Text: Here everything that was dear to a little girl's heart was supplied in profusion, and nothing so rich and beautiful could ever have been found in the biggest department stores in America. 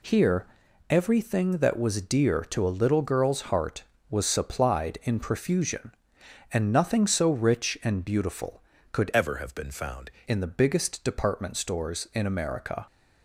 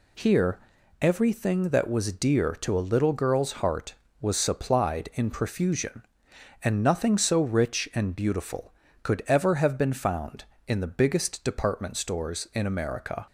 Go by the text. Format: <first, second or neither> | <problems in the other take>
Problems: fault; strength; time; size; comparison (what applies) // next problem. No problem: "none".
second | pauses between "Here" and "everything"; at 0.4 s; 0.44 s long; also in the second // changes voice from "ever" to "found"; from 9.1 to 10.0 s; 0.9 s long